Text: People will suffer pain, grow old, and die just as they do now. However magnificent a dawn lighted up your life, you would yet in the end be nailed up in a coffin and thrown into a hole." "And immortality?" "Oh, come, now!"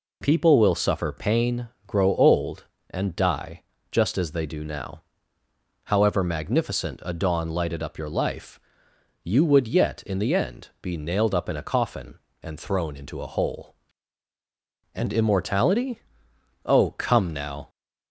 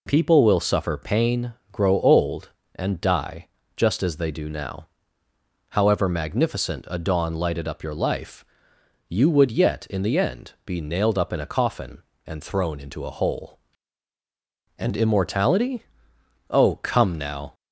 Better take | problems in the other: neither | pauses between "die" and "just"; slight; the same in both

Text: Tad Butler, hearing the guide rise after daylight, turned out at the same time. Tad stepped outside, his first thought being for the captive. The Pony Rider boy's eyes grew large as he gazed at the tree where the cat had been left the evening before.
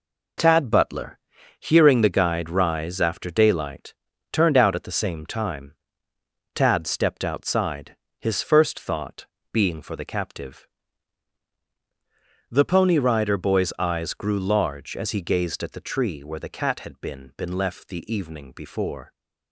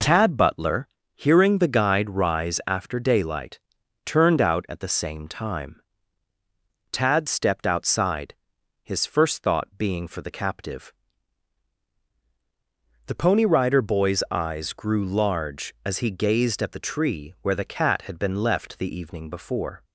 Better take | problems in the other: second | pauses between "thought" and "being"; slight; at 9.2 s; 0.26 s long // says "been" twice; at 17.3 s

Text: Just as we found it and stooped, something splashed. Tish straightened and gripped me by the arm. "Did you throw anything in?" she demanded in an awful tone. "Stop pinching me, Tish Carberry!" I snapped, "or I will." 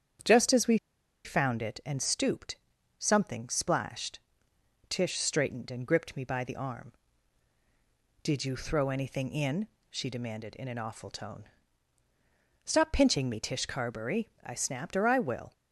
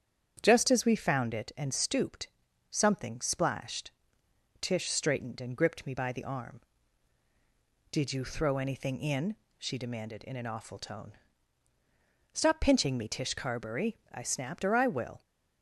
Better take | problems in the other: second | starts louder than the rest; strong; until 1.7 s; 8.5 dB; strong in the second // pauses between "we" and "found"; noticeable; at 0.7 s; 0.48 s long

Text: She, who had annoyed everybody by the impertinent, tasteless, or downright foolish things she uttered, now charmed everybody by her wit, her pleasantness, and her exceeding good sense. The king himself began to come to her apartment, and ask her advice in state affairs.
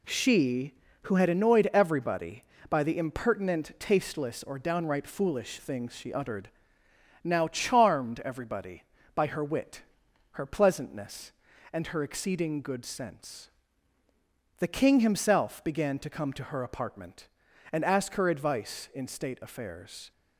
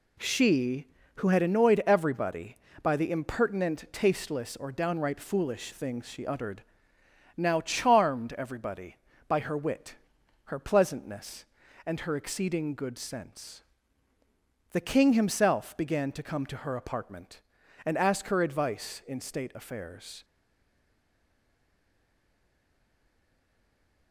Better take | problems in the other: first | stays silent after the last word; strong; from 20.2 s on; 3.9 s long

